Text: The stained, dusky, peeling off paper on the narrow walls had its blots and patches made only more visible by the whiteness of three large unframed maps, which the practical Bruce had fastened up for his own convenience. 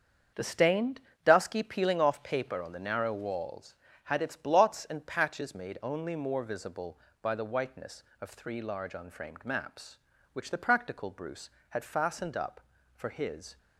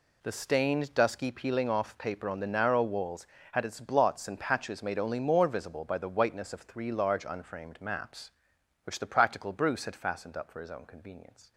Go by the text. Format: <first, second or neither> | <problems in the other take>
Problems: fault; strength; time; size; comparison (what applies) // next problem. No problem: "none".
second | starts louder than the rest; until 1.6 s; 7 dB // stops before "own convenience"; at 13.5 s